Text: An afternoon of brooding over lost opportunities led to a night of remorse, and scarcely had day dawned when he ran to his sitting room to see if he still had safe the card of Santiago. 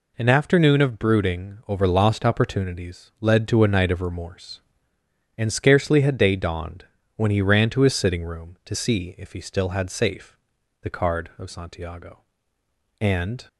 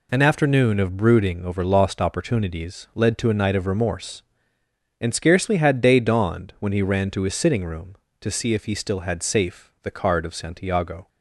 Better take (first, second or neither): second